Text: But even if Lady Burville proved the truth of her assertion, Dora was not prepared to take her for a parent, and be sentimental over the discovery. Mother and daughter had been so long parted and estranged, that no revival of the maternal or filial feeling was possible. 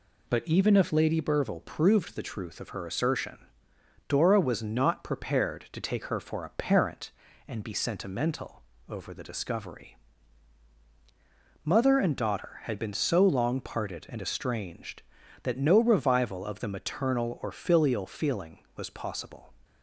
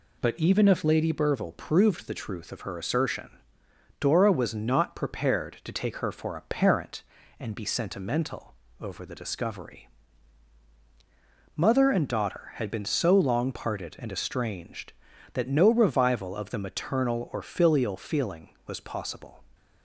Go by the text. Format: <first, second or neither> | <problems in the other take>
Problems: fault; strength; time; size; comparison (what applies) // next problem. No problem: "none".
neither | pauses between "sentimental" and "over"; slight; the same in both